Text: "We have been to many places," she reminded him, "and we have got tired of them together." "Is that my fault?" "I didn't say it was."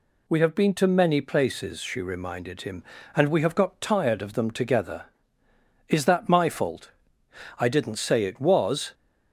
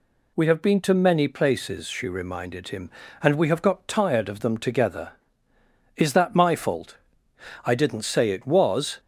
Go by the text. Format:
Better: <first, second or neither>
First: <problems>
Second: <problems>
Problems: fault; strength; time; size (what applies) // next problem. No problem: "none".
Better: neither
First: none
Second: none